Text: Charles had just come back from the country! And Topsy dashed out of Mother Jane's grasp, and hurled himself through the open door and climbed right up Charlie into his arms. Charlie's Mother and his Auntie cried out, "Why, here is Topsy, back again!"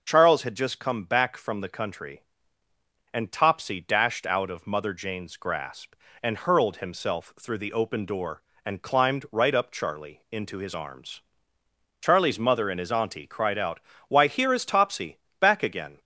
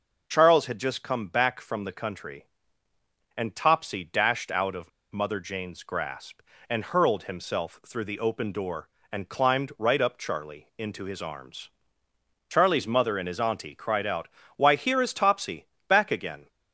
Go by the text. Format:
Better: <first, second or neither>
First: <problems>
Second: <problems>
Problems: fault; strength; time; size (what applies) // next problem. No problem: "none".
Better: first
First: none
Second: pauses between "of" and "Mother"; slight; at 4.8 s; 0.23 s long